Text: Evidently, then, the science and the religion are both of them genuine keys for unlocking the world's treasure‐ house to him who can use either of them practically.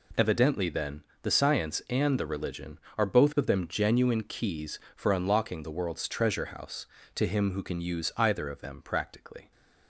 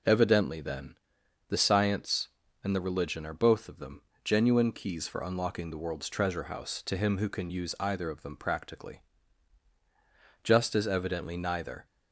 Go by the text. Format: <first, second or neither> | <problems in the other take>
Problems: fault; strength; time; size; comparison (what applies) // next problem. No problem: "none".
first | pauses between "them" and "genuine"; slight; at 4.0 s; 0.22 s long // goes on to say "Just as evidently neither"; from 10.4 s on; 1.4 s long